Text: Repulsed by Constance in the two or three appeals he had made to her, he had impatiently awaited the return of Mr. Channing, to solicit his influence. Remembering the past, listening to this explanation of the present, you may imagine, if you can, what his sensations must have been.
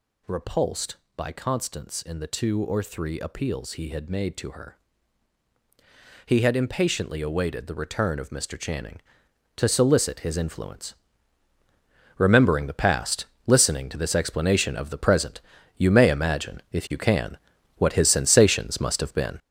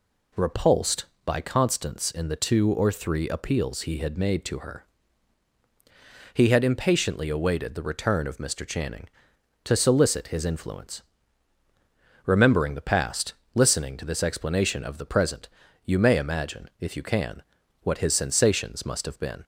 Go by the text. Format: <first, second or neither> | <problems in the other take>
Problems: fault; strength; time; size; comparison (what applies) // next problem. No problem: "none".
second | gets louder; strong; throughout; 7.5 dB